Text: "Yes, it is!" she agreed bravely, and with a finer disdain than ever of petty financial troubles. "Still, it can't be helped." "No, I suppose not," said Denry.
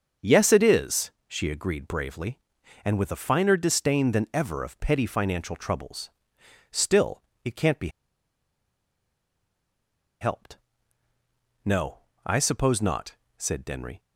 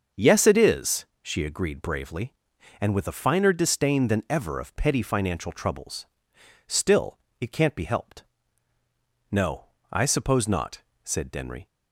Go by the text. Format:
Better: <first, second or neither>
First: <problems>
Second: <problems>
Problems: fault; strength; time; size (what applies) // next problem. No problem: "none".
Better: second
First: starts louder than the rest; until 1.3 s; 6.5 dB // pauses between "be" and "helped"; strong; at 7.8 s; 2.3 s long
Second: starts louder than the rest; until 1.3 s; 6.5 dB